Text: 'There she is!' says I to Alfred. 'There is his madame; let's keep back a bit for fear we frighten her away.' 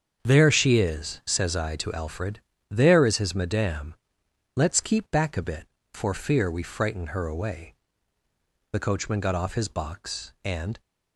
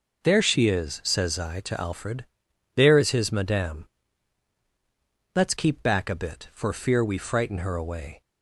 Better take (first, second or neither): second